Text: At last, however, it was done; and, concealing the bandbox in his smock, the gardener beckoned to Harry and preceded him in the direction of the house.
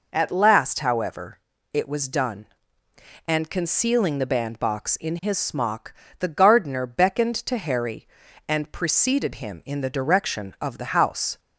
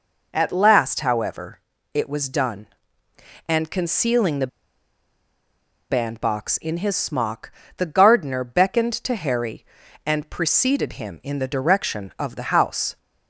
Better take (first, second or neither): first